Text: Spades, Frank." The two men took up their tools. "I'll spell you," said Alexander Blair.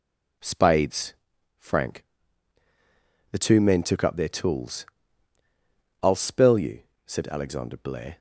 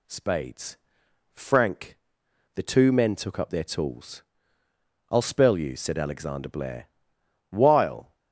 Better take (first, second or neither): first